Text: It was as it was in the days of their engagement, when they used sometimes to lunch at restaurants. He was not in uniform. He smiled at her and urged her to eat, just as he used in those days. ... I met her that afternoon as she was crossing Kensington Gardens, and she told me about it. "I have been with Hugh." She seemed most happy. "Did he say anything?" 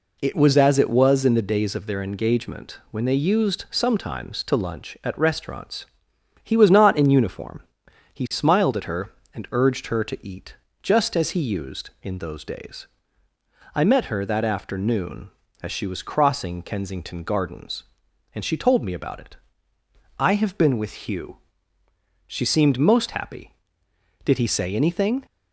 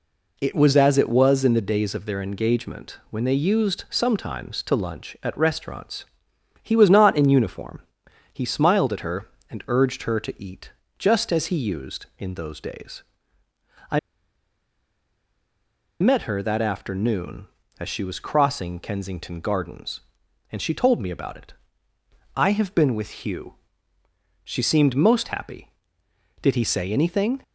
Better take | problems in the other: first | pauses between "I" and "met"; strong; at 13.9 s; 2.0 s long

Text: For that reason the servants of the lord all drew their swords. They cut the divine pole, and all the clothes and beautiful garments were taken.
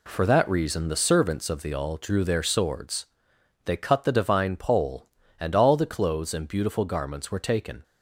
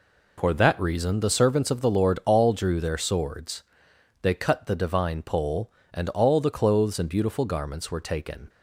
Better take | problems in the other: second | skips "lord"; at 1.7 s

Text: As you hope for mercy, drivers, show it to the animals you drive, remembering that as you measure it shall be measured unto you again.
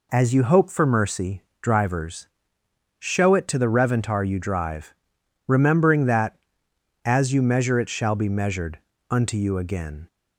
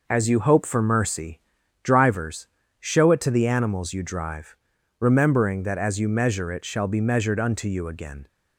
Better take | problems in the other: second | says "reventar" for "animals"; at 3.6 s // pauses between "measured" and "unto"; slight; at 8.7 s; 0.32 s long

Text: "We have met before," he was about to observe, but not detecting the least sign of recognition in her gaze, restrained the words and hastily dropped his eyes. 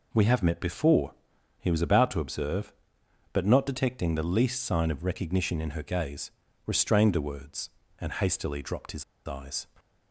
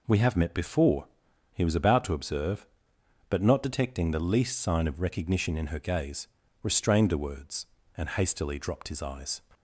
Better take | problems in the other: second | pauses between "his" and "eyes"; slight; at 9.0 s; 0.22 s long

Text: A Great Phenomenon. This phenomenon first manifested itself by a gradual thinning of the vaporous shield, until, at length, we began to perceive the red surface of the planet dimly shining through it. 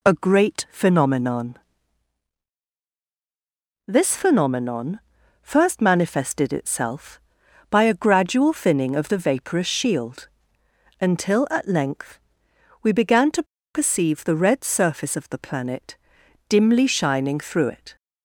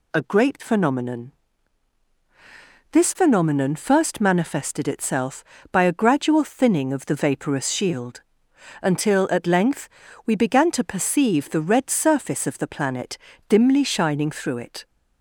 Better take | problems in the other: second | pauses between "phenomenon" and "first"; noticeable; at 4.9 s; 0.46 s long // pauses between "to" and "perceive"; slight; at 13.4 s; 0.30 s long // pauses between "planet" and "dimly"; noticeable; at 15.9 s; 0.52 s long; slight in the second

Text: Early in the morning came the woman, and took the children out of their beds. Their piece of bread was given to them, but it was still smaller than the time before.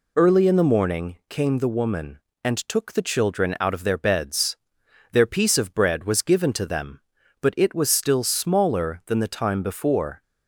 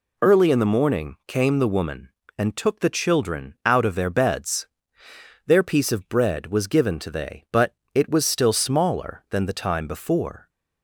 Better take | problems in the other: first | says "they" for "them"; at 7.1 s // pauses between "but" and "it"; slight; at 7.7 s; 0.18 s long

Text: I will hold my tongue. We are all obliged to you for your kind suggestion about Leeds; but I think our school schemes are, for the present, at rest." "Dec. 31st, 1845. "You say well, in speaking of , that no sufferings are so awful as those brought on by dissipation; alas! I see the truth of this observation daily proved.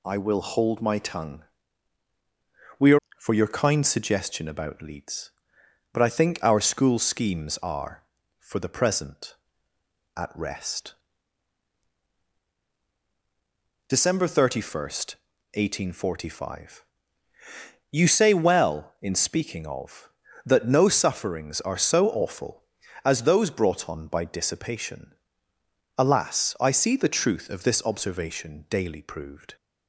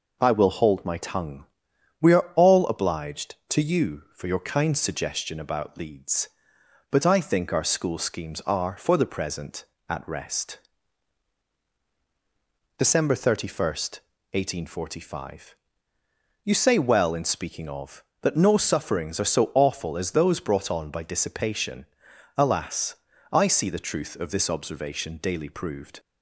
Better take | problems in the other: second | skips "all obliged to you"; at 3.0 s

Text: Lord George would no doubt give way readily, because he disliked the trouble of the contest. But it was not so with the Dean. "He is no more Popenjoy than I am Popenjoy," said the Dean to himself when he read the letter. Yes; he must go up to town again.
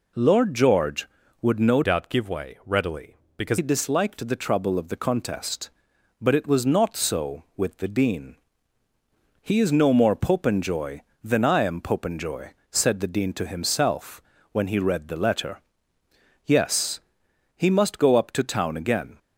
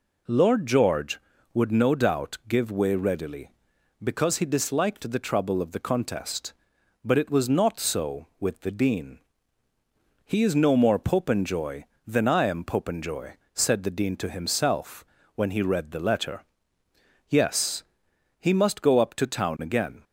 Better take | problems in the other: second | changes voice from "doubt" to "because"; from 1.8 to 3.5 s; 1.7 s long // pauses between "himself" and "when"; slight; at 14.2 s; 0.30 s long; slight in the second

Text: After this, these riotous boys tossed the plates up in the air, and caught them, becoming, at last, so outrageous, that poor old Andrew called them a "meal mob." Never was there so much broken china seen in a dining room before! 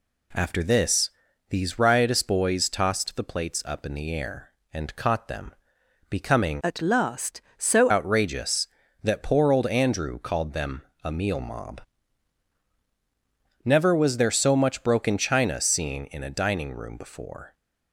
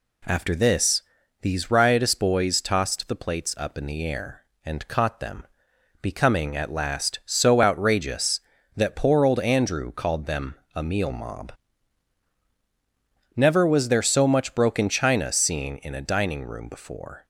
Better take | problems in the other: second | changes voice from "at" to "so"; from 6.6 to 7.9 s; 1.3 s long // pauses between "them" and "a"; slight; at 10.8 s; 0.22 s long; slight in the second

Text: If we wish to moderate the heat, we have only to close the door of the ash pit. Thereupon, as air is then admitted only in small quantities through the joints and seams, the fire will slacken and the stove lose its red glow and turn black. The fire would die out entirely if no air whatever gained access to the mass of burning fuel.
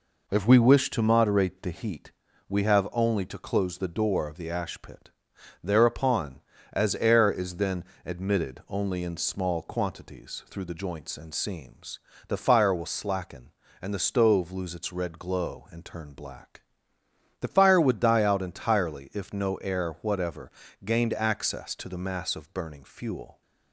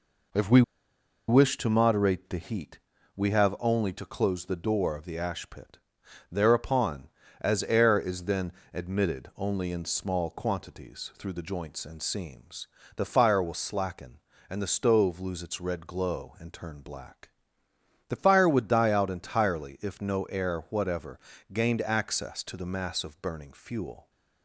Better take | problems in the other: first | pauses between "we" and "wish"; noticeable; at 0.6 s; 0.66 s long // pauses between "then" and "admitted"; slight; at 8.5 s; 0.20 s long; slight in the first // pauses between "whatever" and "gained"; slight; at 21.1 s; 0.34 s long; slight in the first

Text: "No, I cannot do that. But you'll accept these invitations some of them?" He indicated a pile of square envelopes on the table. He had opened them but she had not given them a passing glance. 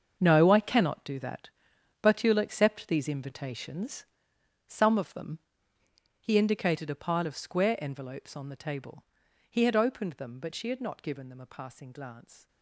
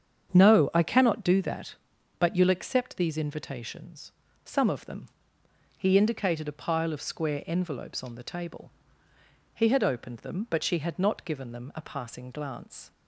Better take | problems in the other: second | gets quieter; strong; throughout; 13.5 dB // starts louder than the rest; until 1.2 s; 6.5 dB; strong in the second // pauses between "invitations" and "some"; noticeable; at 4.0 s; 0.64 s long; slight in the second

